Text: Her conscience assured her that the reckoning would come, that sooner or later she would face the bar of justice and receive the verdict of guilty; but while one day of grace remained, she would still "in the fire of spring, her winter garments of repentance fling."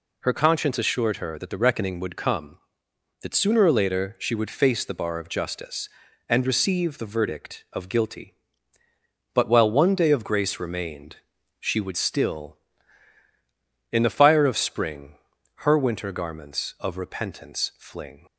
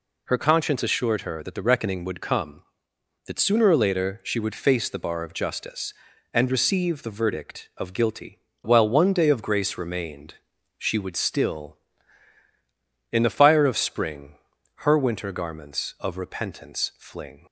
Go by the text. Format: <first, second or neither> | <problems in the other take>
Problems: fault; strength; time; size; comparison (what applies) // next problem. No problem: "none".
first | skips "but"; at 8.5 s